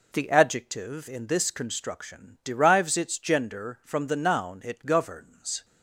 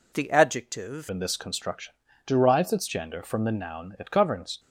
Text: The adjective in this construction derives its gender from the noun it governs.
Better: first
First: none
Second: changes voice at "in"; from 1.0 s on; 3.5 s long // pauses between "construction" and "derives"; slight; at 1.9 s; 0.34 s long

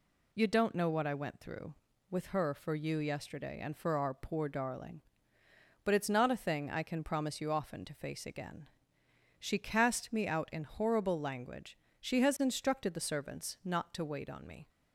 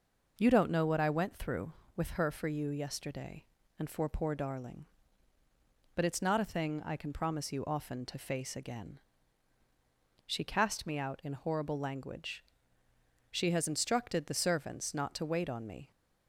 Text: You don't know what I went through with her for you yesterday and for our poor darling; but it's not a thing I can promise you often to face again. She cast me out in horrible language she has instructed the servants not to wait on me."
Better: first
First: pauses between "language" and "she"; slight; at 11.7 s; 0.24 s long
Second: skips "our"; at 4.0 s // pauses between "language" and "she"; noticeable; at 12.4 s; 0.92 s long

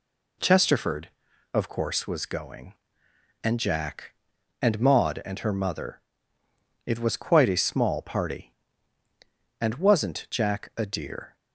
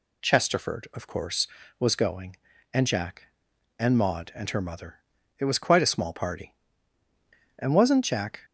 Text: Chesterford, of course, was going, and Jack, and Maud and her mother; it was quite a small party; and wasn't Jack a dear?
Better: first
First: none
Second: stops before "a dear"; at 8.4 s

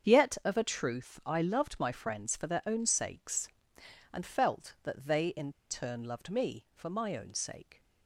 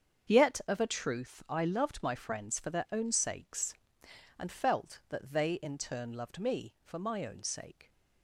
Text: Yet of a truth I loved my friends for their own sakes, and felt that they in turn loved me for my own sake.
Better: second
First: starts louder than the rest; strong; until 1.1 s; 7 dB // pauses between "in" and "turn"; slight; at 5.5 s; 0.18 s long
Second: starts louder than the rest; strong; until 1.3 s; 7 dB

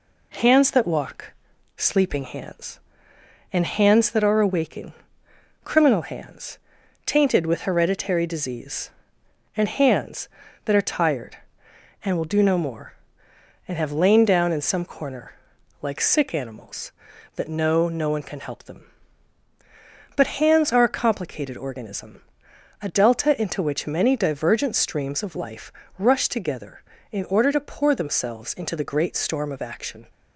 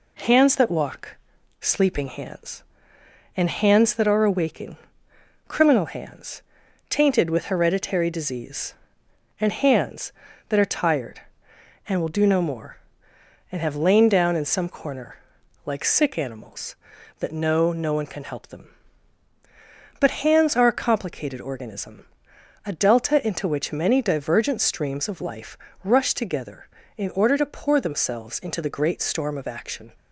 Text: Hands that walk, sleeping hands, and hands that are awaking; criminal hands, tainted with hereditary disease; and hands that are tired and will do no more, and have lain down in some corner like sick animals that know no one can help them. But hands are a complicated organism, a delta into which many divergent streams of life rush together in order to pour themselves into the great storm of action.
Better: neither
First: pauses between "corner" and "like"; noticeable; at 15.3 s; 0.48 s long // pauses between "life" and "rush"; slight; at 25.7 s; 0.26 s long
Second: pauses between "corner" and "like"; noticeable; at 15.1 s; 0.48 s long // pauses between "life" and "rush"; slight; at 25.5 s; 0.26 s long

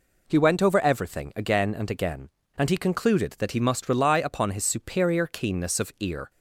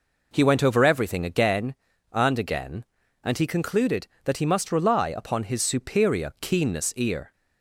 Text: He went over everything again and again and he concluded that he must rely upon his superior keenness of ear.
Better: first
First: none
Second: skips "of"; at 6.9 s

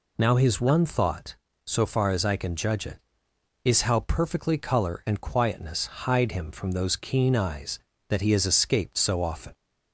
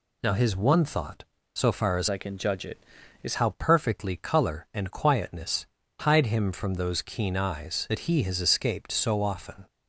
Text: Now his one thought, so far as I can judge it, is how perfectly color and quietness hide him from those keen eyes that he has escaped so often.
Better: first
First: none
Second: changes voice from "I" to "is"; from 2.0 to 3.3 s; 1.3 s long // pauses between "quietness" and "hide"; slight; at 5.6 s; 0.34 s long

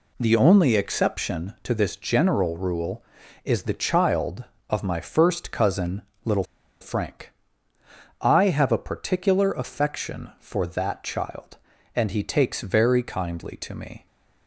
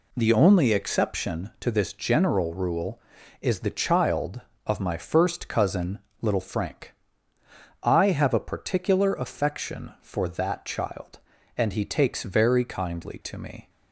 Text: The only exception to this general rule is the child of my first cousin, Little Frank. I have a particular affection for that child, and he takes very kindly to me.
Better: second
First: pauses between "Little" and "Frank"; at 6.4 s; 0.36 s long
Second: none

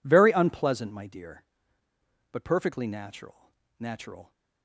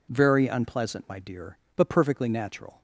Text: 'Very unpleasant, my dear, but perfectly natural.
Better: second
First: says "natural" twice; at 3.7 s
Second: none

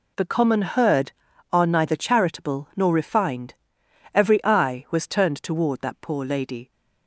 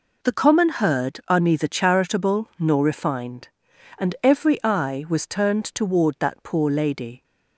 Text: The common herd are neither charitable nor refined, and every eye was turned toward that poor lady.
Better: second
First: skips "and"; at 3.8 s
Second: none

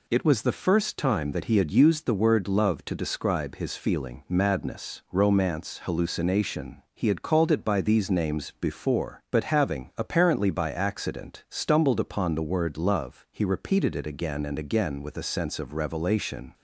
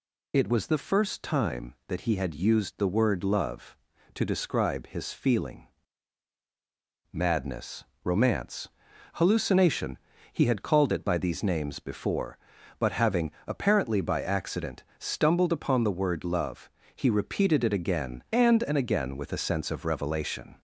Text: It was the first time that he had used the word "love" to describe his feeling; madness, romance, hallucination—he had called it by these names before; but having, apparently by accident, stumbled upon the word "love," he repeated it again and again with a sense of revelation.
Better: first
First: none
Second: says "and" twice; at 18.6 s

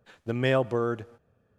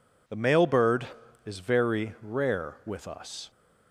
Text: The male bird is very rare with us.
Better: second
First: stops before "is very rare with us"; at 1.1 s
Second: none

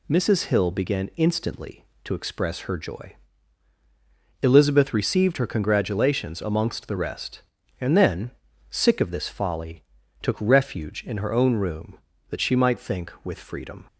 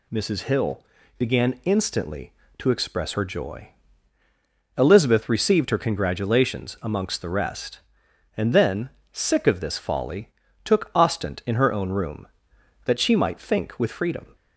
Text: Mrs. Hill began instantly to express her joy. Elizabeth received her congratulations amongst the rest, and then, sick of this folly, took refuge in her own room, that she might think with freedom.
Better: first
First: none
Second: pauses between "Hill" and "began"; slight; at 0.8 s; 0.36 s long // says "ostent" for "refuge"; at 10.9 s

